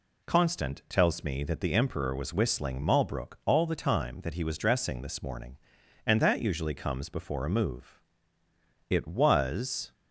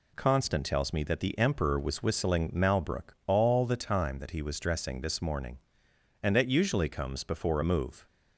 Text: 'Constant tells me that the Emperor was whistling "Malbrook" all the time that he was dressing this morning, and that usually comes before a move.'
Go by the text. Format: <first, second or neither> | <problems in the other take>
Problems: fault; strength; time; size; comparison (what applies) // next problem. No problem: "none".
second | goes on to say "It was"; noticeable; from 8.9 s on; 1.0 s long